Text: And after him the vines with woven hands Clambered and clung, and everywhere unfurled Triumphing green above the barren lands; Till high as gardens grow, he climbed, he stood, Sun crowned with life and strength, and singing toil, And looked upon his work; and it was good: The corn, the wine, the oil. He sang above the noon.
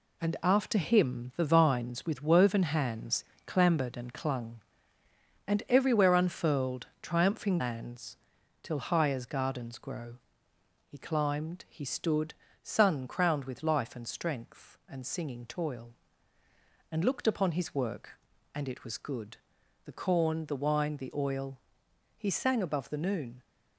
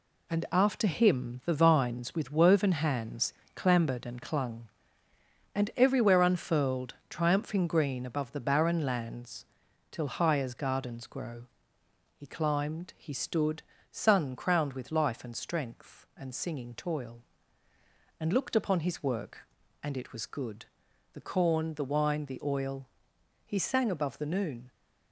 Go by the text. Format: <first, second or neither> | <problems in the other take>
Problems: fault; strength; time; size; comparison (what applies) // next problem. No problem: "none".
second | pauses between "hands" and "Clambered"; slight; at 3.2 s; 0.22 s long; slight in the second // pauses between "unfurled" and "Triumphing"; slight; at 6.8 s; 0.16 s long; slight in the second // skips "green above the barren"; at 7.5 s